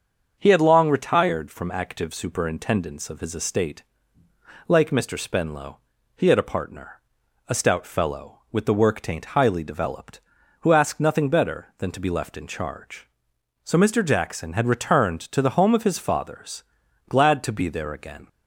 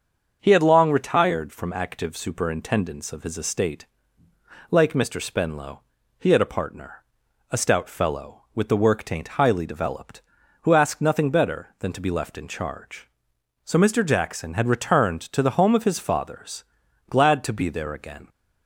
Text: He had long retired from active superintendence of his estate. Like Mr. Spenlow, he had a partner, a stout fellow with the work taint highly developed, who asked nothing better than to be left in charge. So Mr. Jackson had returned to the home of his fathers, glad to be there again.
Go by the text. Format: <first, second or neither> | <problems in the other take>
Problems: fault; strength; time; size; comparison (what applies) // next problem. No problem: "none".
neither | starts louder than the rest; the same in both